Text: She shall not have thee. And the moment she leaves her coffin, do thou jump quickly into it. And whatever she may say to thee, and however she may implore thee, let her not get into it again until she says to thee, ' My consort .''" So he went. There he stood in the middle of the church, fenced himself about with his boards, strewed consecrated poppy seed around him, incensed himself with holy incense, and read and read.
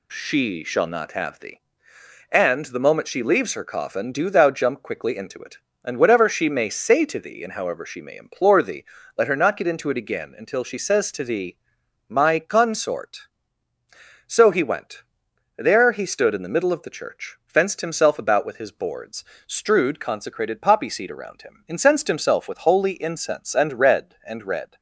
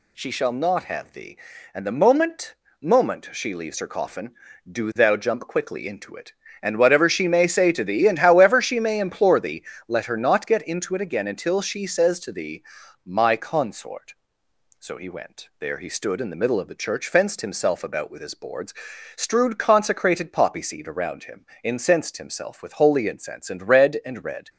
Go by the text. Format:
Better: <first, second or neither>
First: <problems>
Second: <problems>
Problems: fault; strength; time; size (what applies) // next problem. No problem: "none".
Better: first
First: none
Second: says "moment" twice; at 2.8 s